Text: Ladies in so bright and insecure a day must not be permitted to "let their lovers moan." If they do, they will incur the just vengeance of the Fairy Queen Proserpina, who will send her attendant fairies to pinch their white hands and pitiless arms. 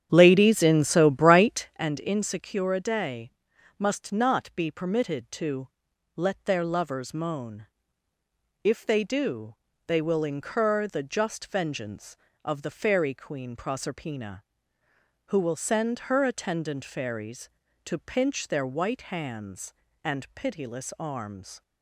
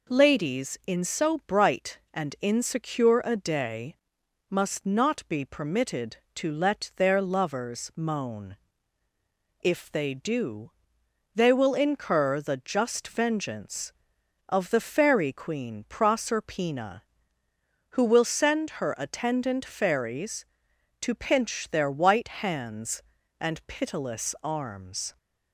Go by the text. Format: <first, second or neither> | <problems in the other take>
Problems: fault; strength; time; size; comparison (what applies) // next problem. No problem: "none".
second | starts louder than the rest; strong; until 1.8 s; 9.5 dB // pauses between "day" and "must"; noticeable; at 3.2 s; 0.48 s long; noticeable in the second // pauses between "to" and "let"; noticeable; at 5.6 s; 0.48 s long